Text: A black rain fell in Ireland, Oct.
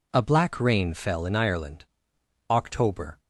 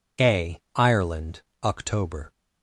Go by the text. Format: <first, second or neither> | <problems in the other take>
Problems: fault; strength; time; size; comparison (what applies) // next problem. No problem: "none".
first | skips "black rain fell in"; at 0.6 s